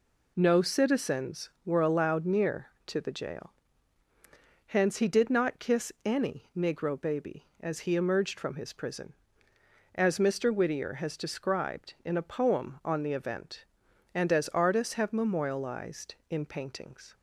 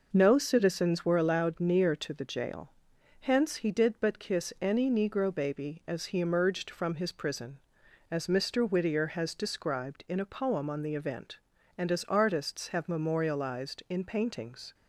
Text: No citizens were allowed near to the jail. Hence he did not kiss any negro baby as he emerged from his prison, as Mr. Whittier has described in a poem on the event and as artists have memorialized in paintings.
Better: first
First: none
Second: says "but" for "not"; at 3.9 s

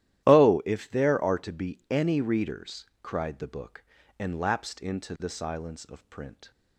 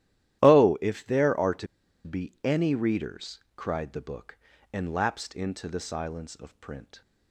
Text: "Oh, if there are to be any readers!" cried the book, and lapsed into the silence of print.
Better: first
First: starts louder than the rest; strong; until 1.2 s; 13 dB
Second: starts louder than the rest; strong; until 1.4 s; 13 dB // pauses between "to" and "be"; at 1.6 s; 0.38 s long

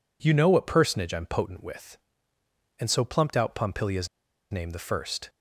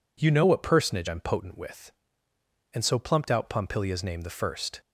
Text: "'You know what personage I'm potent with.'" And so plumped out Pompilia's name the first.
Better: second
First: pauses between "Pompilia's" and "name"; at 4.0 s; 0.44 s long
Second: none

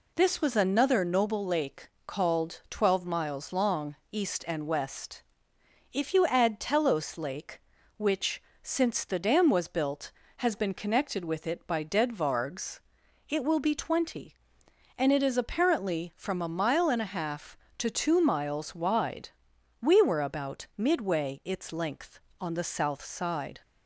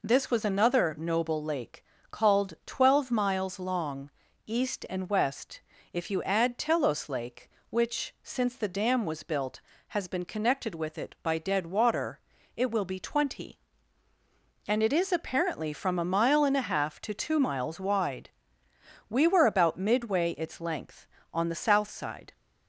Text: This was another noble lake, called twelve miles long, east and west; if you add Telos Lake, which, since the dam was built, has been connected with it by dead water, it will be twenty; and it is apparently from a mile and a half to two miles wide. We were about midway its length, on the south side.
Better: second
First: says "vargs" for "water"; at 12.1 s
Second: none

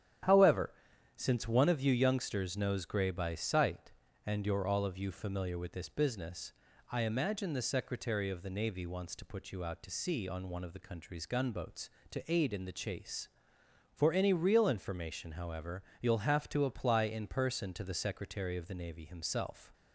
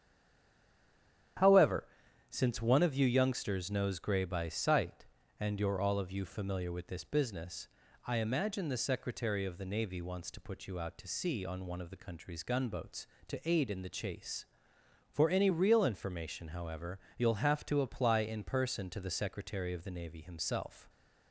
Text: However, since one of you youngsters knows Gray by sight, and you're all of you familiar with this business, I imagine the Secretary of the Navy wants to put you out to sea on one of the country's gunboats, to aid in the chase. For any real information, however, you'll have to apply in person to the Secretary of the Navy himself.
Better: first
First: starts louder than the rest; strong; until 1.7 s; 10.5 dB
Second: stays silent before the first word; noticeable; until 1.3 s; 1.3 s long // starts louder than the rest; strong; until 2.8 s; 10.5 dB

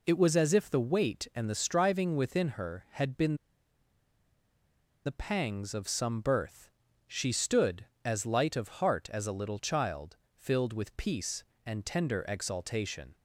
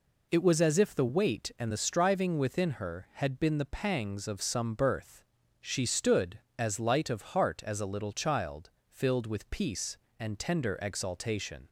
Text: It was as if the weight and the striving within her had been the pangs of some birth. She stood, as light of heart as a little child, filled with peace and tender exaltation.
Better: second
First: pauses between "been" and "the"; strong; at 3.3 s; 1.6 s long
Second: none

